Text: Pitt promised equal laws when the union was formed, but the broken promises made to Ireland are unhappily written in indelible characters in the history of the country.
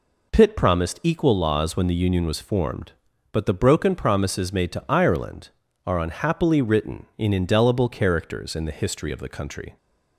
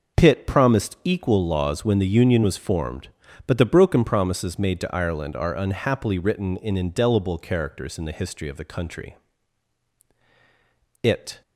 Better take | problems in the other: first | goes on to say "It"; slight; from 11.0 s on; 0.40 s long

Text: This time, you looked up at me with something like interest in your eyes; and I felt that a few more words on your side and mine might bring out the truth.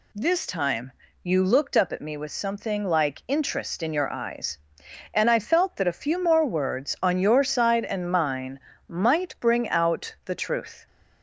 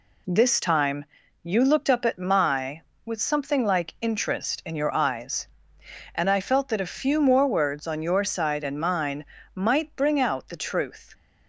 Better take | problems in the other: first | says "my" for "me"; at 2.1 s // pauses between "mine" and "might"; slight; at 9.2 s; 0.30 s long; slight in the first

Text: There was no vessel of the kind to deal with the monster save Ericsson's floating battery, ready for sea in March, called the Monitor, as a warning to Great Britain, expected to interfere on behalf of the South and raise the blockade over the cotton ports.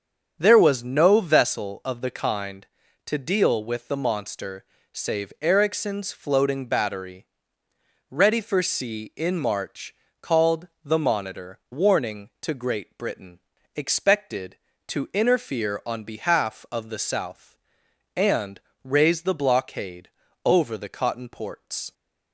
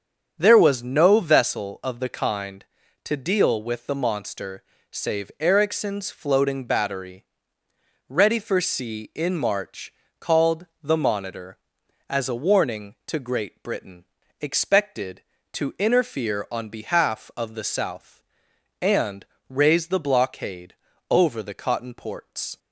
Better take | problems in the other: second | starts louder than the rest; strong; until 1.4 s; 7.5 dB; strong in the second // pauses between "monster" and "save"; slight; at 4.6 s; 0.28 s long; slight in the second // pauses between "called" and "the"; slight; at 10.6 s; 0.16 s long; slight in the second // skips "as a"; at 11.6 s // pauses between "and" and "raise"; slight; at 18.5 s; 0.24 s long; slight in the second // pauses between "blockade" and "over"; slight; at 20.0 s; 0.34 s long; slight in the second

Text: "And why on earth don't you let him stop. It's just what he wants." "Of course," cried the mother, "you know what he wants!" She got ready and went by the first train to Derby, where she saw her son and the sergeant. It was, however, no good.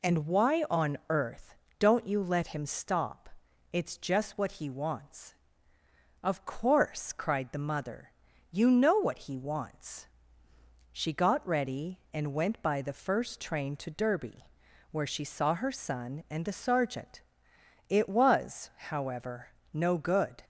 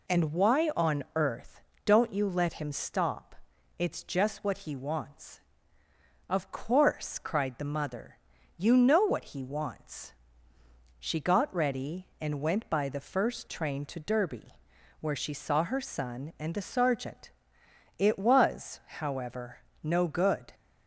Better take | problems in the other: neither | pauses between "earth" and "don't"; slight; the same in both

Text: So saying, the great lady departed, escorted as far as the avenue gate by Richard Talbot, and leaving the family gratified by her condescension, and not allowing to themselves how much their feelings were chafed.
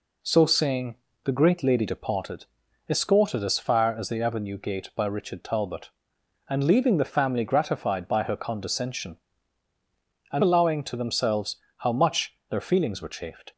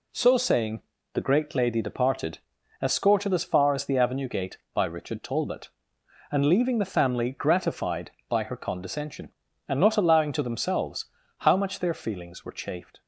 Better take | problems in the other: second | skips "not"; at 10.4 s // pauses between "themselves" and "how"; slight; at 11.5 s; 0.22 s long; slight in the second // pauses between "much" and "their"; slight; at 12.3 s; 0.16 s long

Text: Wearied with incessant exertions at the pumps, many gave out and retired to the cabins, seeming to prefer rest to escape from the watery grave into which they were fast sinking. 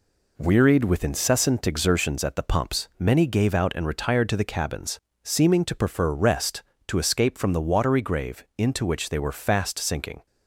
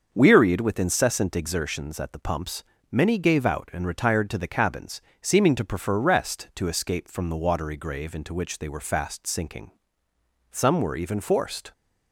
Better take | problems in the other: first | starts louder than the rest; until 1.1 s; 6.5 dB // goes on to say "Some were even forced"; noticeable; from 10.5 s on; 1.2 s long

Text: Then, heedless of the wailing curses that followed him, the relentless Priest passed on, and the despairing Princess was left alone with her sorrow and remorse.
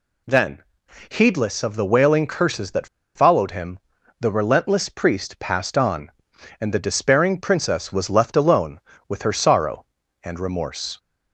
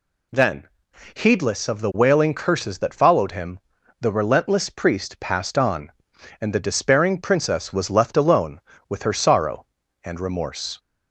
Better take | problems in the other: second | pauses between "that" and "followed"; slight; at 2.8 s; 0.29 s long

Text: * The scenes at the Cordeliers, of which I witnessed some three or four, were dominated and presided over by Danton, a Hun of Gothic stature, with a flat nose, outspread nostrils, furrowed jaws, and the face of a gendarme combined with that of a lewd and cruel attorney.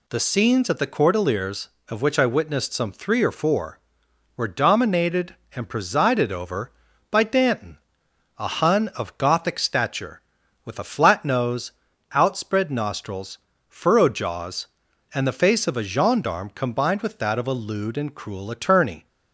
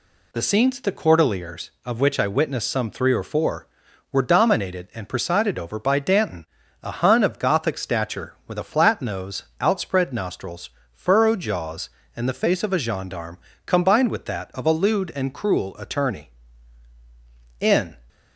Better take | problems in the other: first | pauses between "gendarme" and "combined"; slight; at 13.3 s; 0.28 s long // goes on to say "In"; slight; from 17.5 s on; 0.38 s long

